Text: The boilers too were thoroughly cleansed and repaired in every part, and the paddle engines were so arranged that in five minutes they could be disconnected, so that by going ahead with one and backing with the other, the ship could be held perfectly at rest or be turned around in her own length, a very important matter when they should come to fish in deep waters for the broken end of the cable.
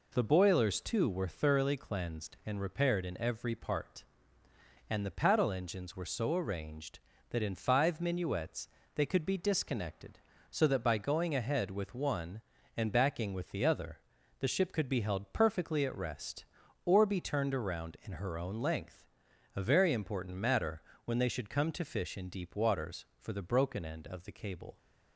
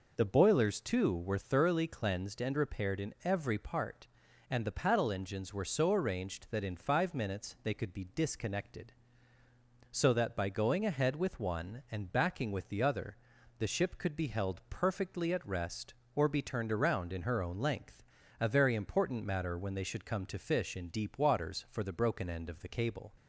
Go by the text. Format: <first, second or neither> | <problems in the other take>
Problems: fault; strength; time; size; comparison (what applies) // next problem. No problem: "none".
second | says "minuets" for "minutes"; at 7.9 s // pauses between "matter" and "when"; slight; at 20.8 s; 0.22 s long